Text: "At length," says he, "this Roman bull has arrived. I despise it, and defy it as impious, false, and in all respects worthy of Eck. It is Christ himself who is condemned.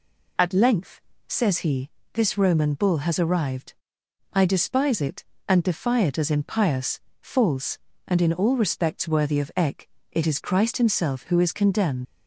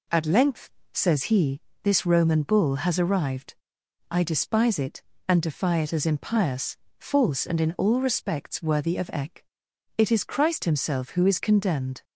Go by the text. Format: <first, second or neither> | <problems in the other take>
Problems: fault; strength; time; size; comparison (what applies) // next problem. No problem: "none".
second | leaves "condemned" unfinished; at 12.0 s; 70 ms